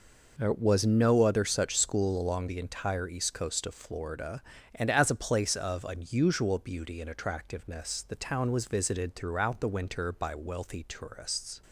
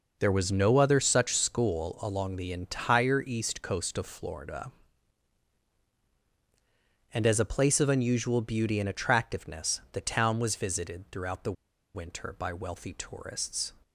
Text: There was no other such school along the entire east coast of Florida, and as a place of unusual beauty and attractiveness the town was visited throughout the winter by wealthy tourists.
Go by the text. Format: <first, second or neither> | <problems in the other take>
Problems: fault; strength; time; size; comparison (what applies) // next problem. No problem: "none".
first | pauses between "the" and "winter"; at 11.5 s; 0.41 s long